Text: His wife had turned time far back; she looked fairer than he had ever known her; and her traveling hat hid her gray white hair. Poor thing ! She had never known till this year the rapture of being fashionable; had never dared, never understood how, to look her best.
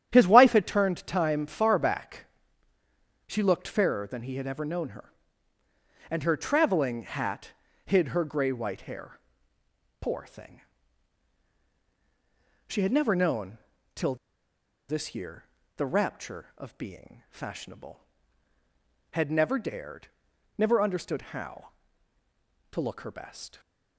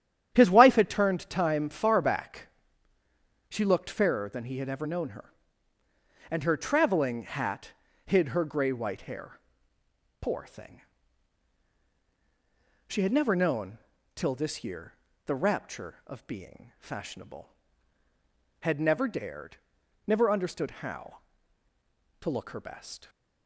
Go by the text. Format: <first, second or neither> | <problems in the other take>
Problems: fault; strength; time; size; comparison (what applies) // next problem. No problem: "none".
second | starts louder than the rest; strong; until 1.1 s; 10 dB; strong in the second // pauses between "hat" and "hid"; slight; at 7.5 s; 0.34 s long; slight in the second // pauses between "known" and "till"; slight; at 13.5 s; 0.34 s long; slight in the second // pauses between "till" and "this"; noticeable; at 14.1 s; 0.73 s long // pauses between "year" and "the"; slight; at 15.4 s; 0.32 s long; slight in the second